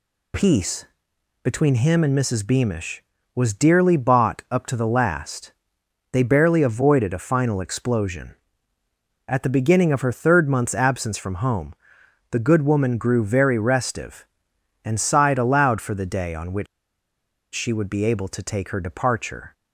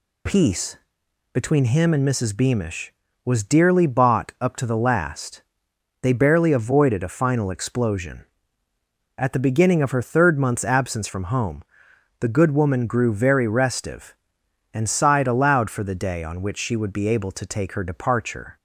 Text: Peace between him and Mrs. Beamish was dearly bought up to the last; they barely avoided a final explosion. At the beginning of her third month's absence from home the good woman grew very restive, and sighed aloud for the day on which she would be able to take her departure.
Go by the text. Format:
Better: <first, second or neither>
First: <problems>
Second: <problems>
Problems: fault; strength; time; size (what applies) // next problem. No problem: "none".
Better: second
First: pauses between "Peace" and "between"; noticeable; at 0.8 s; 0.60 s long // pauses between "home" and "the"; noticeable; at 11.7 s; 0.58 s long // pauses between "which" and "she"; noticeable; at 16.6 s; 0.86 s long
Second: pauses between "Peace" and "between"; noticeable; at 0.7 s; 0.58 s long // pauses between "home" and "the"; noticeable; at 11.6 s; 0.58 s long